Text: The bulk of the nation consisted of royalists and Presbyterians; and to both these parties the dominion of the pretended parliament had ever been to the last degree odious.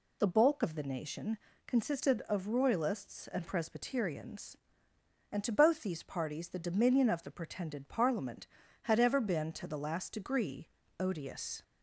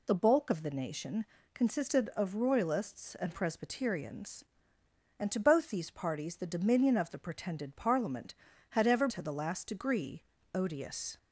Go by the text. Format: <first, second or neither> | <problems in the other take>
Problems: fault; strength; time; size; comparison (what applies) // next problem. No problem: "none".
first | pauses between "nation" and "consisted"; slight; at 1.2 s; 0.28 s long; slight in the first // skips "been"; at 9.0 s // pauses between "degree" and "odious"; slight; at 10.2 s; 0.30 s long; slight in the first